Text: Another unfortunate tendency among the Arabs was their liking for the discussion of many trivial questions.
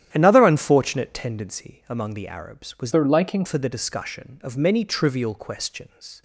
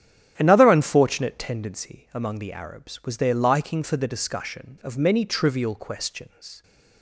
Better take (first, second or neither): second